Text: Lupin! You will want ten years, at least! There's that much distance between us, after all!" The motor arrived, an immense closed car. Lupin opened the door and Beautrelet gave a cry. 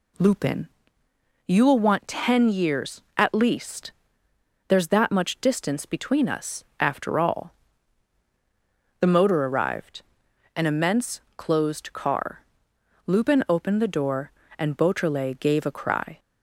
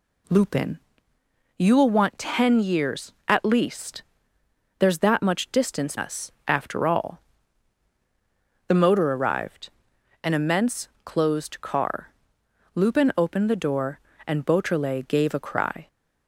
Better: first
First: pauses between "immense" and "closed"; slight; at 11.1 s; 0.16 s long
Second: skips "between"; at 5.9 s // pauses between "immense" and "closed"; slight; at 10.8 s; 0.16 s long

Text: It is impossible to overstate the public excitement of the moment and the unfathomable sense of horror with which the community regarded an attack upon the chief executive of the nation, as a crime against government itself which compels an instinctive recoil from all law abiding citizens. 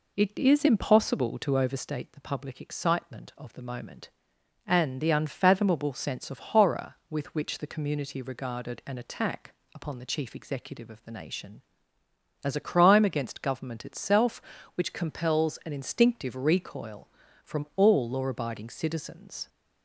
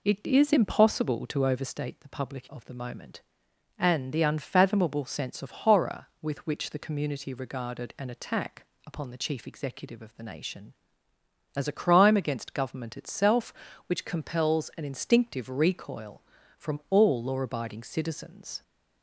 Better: first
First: pauses between "attack" and "upon"; slight; at 9.5 s; 0.20 s long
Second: skips "excitement"; at 2.4 s // pauses between "attack" and "upon"; slight; at 8.6 s; 0.20 s long

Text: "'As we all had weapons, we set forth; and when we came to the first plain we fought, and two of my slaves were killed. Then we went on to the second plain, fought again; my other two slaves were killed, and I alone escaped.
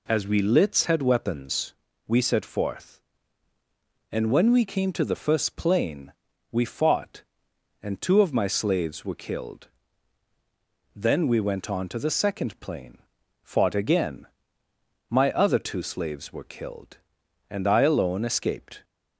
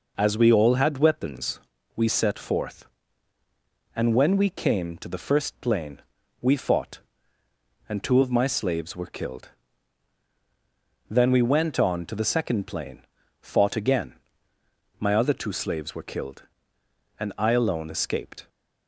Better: second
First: says "lits" for "all"; at 0.4 s // pauses between "plain" and "we"; at 6.1 s; 0.40 s long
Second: pauses between "plain" and "we"; at 6.0 s; 0.40 s long

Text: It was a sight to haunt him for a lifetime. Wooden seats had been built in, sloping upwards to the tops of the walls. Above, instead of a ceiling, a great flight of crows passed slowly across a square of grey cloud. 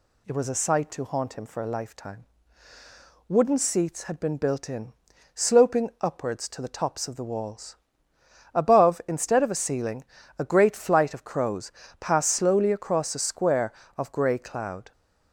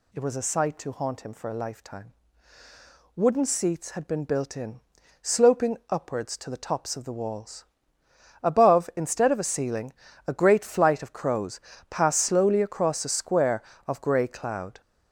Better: first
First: pauses between "crows" and "passed"; slight; at 11.7 s; 0.28 s long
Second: gets louder; strong; throughout; 7 dB // pauses between "crows" and "passed"; slight; at 11.5 s; 0.30 s long

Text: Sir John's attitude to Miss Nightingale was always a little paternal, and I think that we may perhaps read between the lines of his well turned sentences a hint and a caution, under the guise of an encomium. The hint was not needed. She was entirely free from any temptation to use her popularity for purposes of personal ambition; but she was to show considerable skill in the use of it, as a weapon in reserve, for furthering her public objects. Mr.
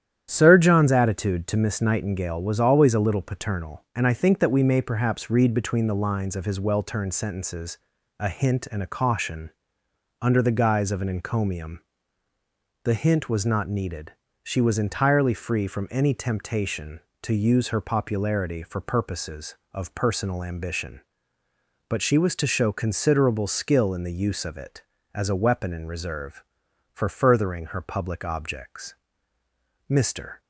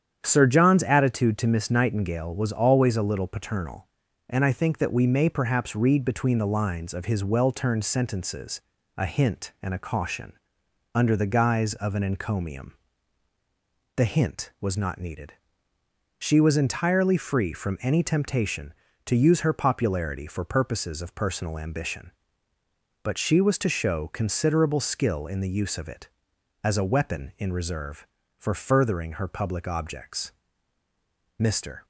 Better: neither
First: starts louder than the rest; strong; until 1.3 s; 10 dB // pauses between "sentences" and "a"; at 7.7 s; 0.40 s long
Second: starts louder than the rest; strong; until 1.2 s; 9 dB // pauses between "sentences" and "a"; slight; at 8.6 s; 0.36 s long

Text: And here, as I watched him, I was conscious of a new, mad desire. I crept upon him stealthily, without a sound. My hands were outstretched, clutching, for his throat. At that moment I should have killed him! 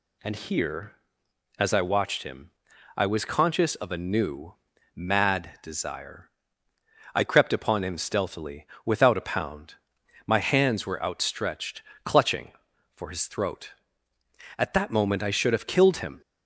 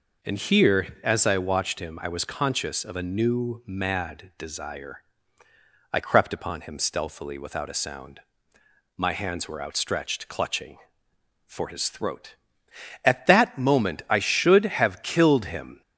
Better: second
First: says "pound" for "sound"; at 9.2 s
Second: none

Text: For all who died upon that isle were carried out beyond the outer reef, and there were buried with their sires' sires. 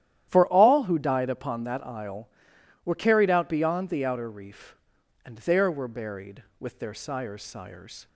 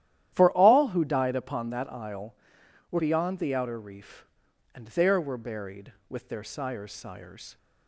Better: first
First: starts louder than the rest; strong; until 1.3 s; 12 dB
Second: starts louder than the rest; strong; until 1.3 s; 12 dB // skips "carried out"; at 2.9 s

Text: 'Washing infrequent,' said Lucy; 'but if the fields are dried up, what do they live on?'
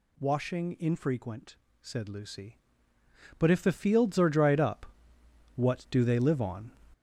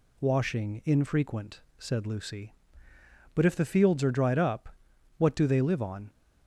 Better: second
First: gets louder; strong; throughout; 7.5 dB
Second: none

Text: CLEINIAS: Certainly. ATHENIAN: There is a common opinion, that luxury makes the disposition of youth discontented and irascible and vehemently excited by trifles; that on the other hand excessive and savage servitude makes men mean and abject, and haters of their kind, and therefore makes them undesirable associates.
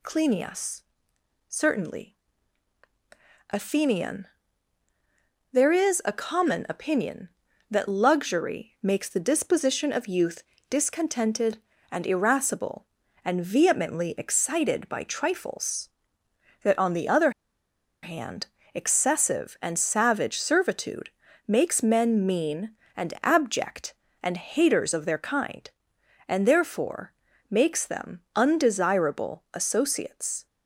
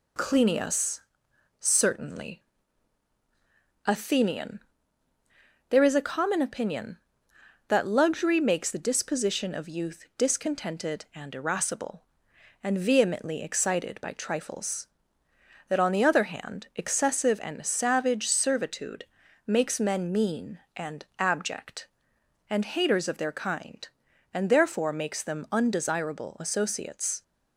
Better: second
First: pauses between "youth" and "discontented"; slight; at 10.4 s; 0.24 s long // pauses between "other" and "hand"; noticeable; at 17.2 s; 0.72 s long // pauses between "hand" and "excessive"; slight; at 18.4 s; 0.28 s long // pauses between "servitude" and "makes"; slight; at 21.0 s; 0.36 s long // pauses between "therefore" and "makes"; at 27.1 s; 0.38 s long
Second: pauses between "servitude" and "makes"; at 19.0 s; 0.42 s long

